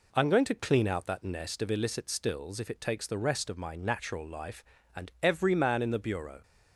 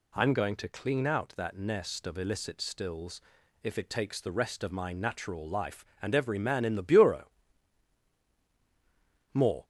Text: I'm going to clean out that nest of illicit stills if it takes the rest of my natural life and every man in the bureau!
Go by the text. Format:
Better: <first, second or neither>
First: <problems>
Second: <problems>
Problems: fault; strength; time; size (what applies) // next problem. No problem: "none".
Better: first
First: none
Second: pauses between "stills" and "if"; at 3.2 s; 0.42 s long // goes on to say "More"; slight; from 9.3 s on; 0.32 s long